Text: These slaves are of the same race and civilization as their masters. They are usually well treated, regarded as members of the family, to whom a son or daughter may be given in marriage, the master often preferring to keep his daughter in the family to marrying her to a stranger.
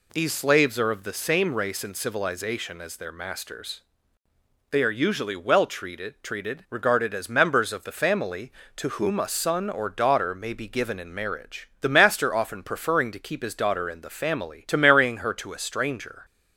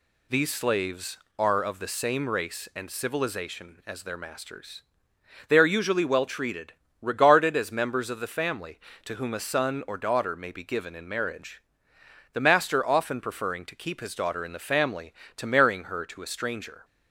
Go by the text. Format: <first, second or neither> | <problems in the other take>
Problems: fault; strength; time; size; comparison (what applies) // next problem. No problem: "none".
second | says "treated" twice; at 6.2 s